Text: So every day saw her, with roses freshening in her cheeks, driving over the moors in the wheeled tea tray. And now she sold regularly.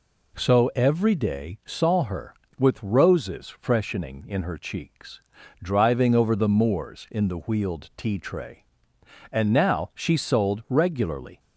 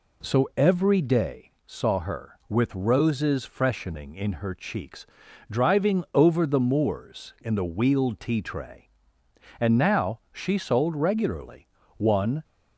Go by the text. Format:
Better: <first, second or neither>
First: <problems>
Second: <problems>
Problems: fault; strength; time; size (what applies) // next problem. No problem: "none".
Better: first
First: none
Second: pauses between "day" and "saw"; slight; at 1.4 s; 0.16 s long // goes on to say "One"; slight; from 11.9 s on; 0.46 s long